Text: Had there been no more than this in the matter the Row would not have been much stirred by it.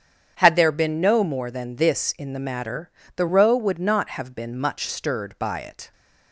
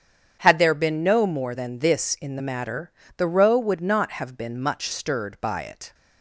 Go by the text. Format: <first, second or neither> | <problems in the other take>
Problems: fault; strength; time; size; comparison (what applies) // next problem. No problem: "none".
neither | starts louder than the rest; strong; the same in both // pauses between "matter" and "the"; slight; the same in both